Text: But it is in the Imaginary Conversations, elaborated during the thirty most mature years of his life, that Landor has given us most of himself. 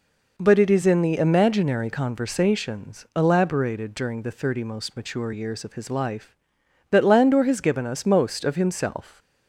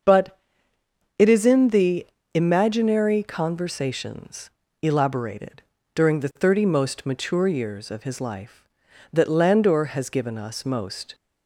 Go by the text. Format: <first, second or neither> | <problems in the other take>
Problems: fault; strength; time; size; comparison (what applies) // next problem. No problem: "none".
first | starts louder than the rest; until 1.8 s; 6.5 dB // pauses between "But" and "it"; noticeable; at 0.3 s; 0.80 s long // pauses between "the" and "Imaginary"; slight; at 2.0 s; 0.26 s long // pauses between "elaborated" and "during"; slight; at 5.6 s; 0.32 s long // stops before "of himself"; at 11.1 s